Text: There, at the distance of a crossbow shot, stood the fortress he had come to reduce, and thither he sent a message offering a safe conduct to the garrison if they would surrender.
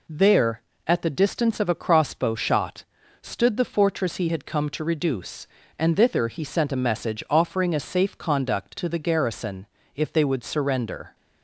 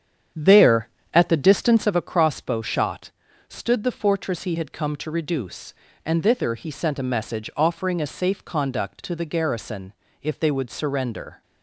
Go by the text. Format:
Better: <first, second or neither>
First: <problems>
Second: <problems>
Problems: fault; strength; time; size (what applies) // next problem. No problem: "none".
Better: first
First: pauses between "garrison" and "if"; slight; at 9.6 s; 0.30 s long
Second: starts louder than the rest; strong; until 2.1 s; 8.5 dB // pauses between "garrison" and "if"; slight; at 9.9 s; 0.30 s long